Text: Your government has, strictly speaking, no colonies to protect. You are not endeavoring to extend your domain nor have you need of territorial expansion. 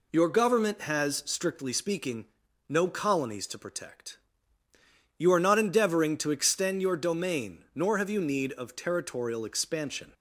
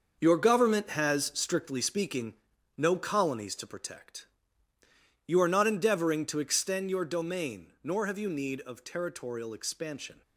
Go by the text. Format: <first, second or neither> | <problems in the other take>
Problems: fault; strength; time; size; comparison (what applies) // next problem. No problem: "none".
first | gets quieter; strong; throughout; 9 dB